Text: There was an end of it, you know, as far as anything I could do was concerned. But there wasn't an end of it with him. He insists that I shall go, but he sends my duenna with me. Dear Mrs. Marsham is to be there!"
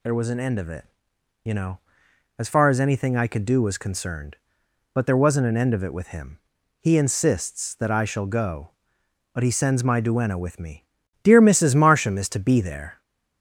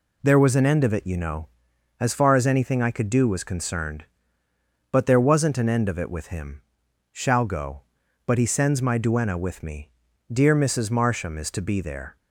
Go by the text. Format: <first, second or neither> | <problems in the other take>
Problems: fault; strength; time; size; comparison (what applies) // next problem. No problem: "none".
first | skips "He insists that I"; at 6.8 s